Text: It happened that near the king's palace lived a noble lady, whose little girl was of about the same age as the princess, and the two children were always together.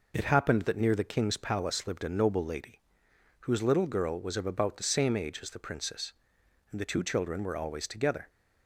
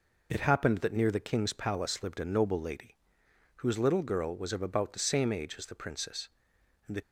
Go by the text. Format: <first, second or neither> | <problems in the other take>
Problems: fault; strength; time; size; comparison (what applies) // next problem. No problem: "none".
first | stops before "two children were always together"; at 7.0 s